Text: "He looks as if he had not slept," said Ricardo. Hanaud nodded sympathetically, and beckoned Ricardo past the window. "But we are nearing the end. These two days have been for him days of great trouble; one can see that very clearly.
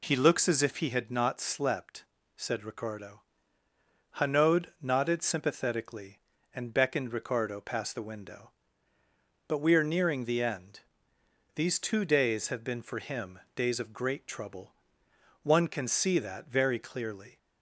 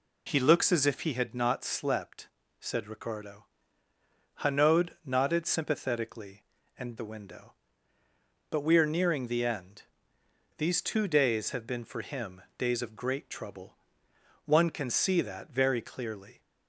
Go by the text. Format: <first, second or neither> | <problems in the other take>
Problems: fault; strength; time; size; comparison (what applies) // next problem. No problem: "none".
first | pauses between "Hanaud" and "nodded"; slight; at 4.8 s; 0.16 s long; slight in the first // skips "beckoned Ricardo past"; at 6.9 s // pauses between "him" and "days"; slight; at 12.4 s; 0.16 s long; slight in the first